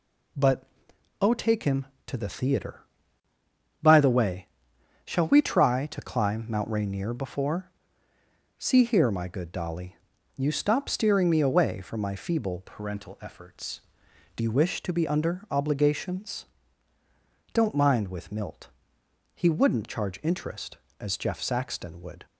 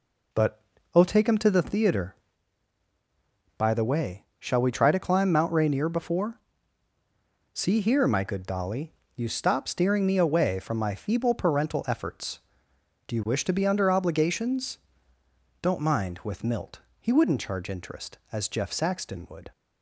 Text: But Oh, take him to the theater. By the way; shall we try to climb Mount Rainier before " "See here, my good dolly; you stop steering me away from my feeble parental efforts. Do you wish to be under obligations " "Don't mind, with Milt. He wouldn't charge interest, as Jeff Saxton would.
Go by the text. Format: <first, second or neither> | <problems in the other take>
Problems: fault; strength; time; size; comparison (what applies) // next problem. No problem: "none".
second | pauses between "But" and "Oh"; noticeable; at 0.6 s; 0.56 s long; slight in the second // changes voice from "parental" to "Do"; from 12.6 to 14.4 s; 1.8 s long